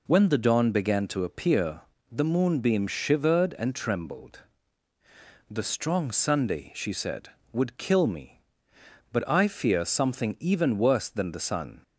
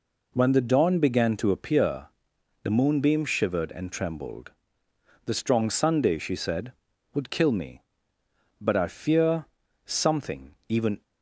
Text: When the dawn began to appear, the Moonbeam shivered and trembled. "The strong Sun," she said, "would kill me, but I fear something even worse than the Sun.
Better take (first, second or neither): first